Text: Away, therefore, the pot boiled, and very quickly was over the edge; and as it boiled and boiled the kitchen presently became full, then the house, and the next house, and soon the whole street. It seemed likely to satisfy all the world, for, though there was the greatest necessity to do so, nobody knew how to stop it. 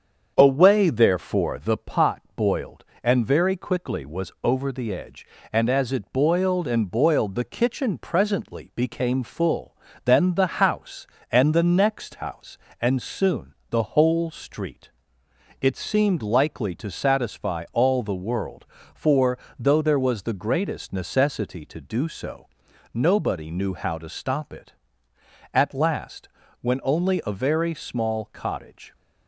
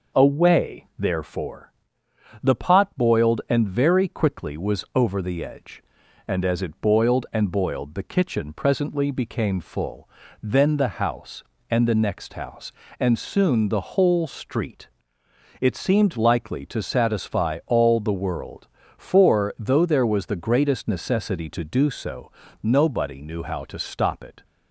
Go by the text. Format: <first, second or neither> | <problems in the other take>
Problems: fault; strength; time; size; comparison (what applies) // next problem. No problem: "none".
second | starts louder than the rest; strong; until 1.3 s; 7.5 dB // pauses between "soon" and "the"; slight; at 13.5 s; 0.16 s long // goes on to say "At last when only a very small cottage"; strong; from 25.5 s on; 3.4 s long